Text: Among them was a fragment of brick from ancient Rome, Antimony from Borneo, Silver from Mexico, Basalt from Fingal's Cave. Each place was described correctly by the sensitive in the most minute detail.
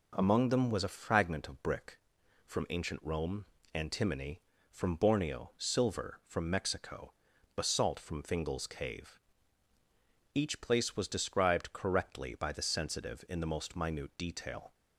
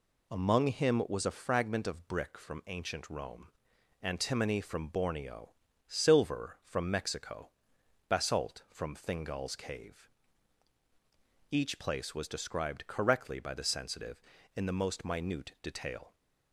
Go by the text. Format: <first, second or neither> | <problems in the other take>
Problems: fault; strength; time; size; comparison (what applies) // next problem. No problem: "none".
first | says "him" for "them"; at 0.6 s